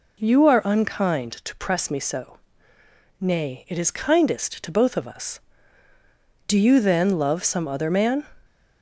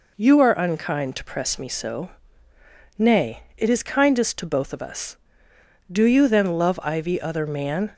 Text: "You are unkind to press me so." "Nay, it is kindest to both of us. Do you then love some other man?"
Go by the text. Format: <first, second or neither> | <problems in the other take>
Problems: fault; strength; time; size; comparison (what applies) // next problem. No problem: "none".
first | says "ivy" for "some"; at 6.8 s